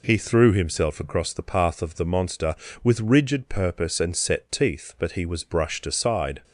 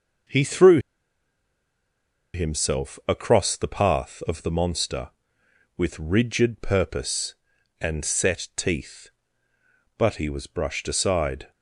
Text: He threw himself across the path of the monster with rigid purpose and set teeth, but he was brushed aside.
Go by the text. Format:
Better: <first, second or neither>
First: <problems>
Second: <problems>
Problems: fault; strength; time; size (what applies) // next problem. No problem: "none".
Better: first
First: none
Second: pauses between "threw" and "himself"; strong; at 0.7 s; 1.5 s long